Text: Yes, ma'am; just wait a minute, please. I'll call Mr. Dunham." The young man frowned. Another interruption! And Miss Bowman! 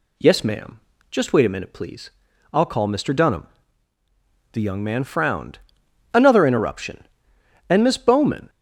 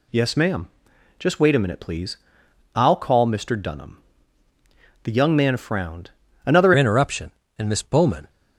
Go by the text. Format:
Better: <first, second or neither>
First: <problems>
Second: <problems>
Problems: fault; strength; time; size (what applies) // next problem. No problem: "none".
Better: first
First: none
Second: changes voice at "interruption"; from 6.7 s on; 1.5 s long